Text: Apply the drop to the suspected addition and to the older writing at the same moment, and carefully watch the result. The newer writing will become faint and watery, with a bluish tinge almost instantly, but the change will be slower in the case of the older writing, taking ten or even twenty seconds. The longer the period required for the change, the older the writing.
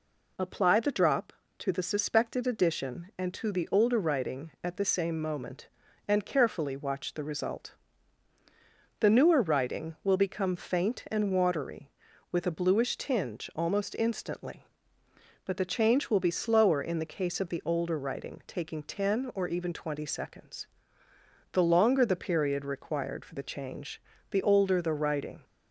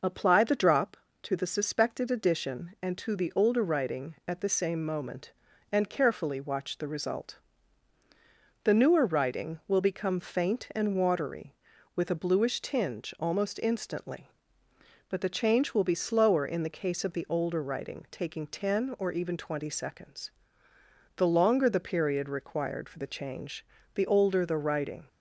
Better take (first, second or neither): first